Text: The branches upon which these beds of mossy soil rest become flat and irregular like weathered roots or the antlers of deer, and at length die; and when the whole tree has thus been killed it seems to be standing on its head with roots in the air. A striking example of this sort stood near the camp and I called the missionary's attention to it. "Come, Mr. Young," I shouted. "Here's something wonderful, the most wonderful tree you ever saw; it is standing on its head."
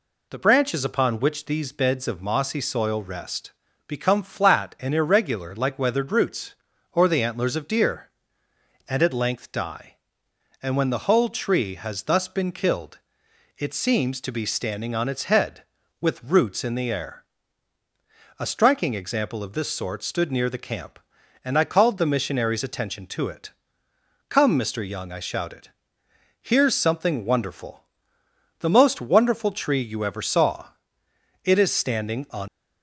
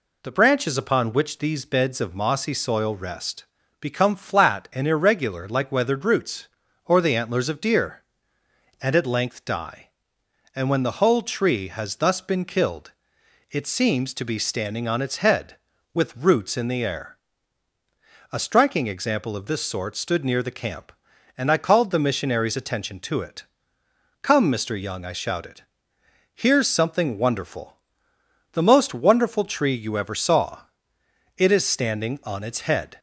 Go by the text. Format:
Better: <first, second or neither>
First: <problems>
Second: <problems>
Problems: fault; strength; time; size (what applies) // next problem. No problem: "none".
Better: second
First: pauses between "rest" and "become"; slight; at 3.5 s; 0.34 s long // pauses between "killed" and "it"; noticeable; at 12.9 s; 0.60 s long // stops before "its head"; at 32.4 s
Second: pauses between "rest" and "become"; slight; at 3.4 s; 0.34 s long // pauses between "killed" and "it"; noticeable; at 12.9 s; 0.60 s long